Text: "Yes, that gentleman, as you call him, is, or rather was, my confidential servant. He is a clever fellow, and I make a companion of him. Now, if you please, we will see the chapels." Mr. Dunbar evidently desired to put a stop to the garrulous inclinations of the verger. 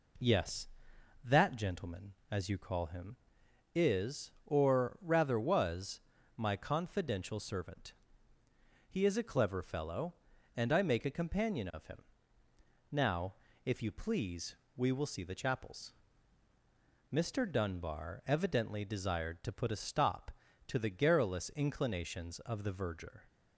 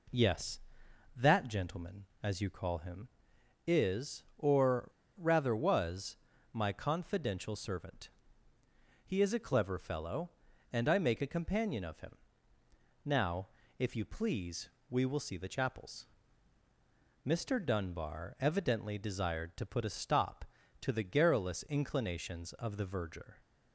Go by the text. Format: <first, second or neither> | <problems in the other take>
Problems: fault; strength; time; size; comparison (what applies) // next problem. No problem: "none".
first | pauses between "or" and "rather"; slight; at 4.8 s; 0.30 s long